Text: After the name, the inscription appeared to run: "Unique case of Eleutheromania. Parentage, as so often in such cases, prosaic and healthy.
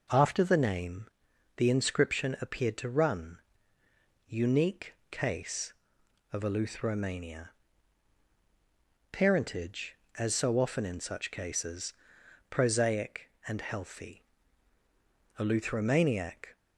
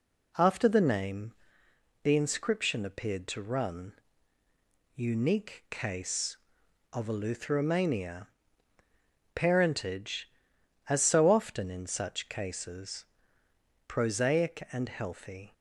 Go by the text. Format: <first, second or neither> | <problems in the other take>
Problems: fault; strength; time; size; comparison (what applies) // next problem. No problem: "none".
second | pauses between "Unique" and "case"; slight; at 4.9 s; 0.16 s long // goes on to say "Eleutheromaniac"; noticeable; from 15.3 s on; 1.1 s long